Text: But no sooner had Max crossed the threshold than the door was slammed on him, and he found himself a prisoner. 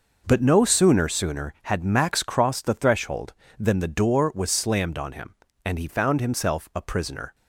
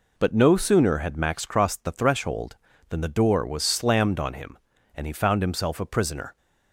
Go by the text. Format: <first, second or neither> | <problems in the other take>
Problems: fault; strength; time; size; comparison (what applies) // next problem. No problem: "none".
second | says "sooner" twice; at 1.0 s